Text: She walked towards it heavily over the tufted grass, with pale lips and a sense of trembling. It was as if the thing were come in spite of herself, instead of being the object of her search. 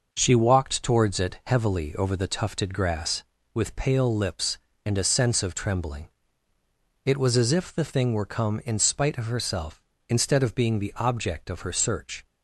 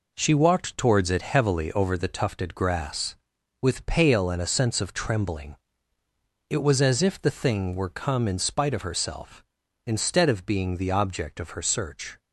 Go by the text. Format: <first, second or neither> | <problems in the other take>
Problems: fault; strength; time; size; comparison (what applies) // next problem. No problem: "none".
first | skips "lips"; at 4.2 s